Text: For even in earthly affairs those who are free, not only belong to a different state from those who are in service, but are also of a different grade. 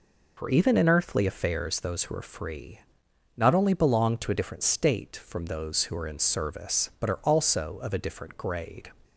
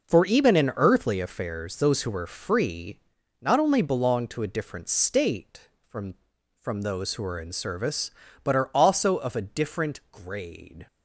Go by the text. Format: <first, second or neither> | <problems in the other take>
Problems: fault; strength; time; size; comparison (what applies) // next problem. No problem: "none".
first | says "from" twice; at 6.6 s